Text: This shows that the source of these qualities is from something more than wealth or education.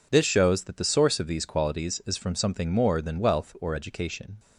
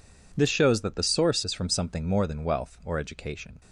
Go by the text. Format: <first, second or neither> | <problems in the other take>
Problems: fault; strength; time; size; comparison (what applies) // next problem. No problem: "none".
first | skips "of these qualities"; at 1.4 s